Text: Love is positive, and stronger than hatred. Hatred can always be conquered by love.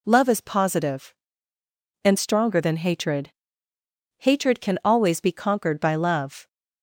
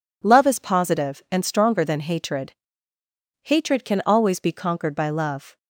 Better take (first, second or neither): neither